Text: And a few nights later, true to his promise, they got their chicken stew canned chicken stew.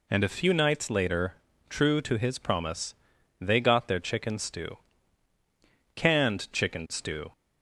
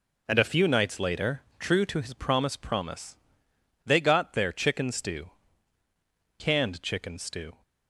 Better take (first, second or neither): first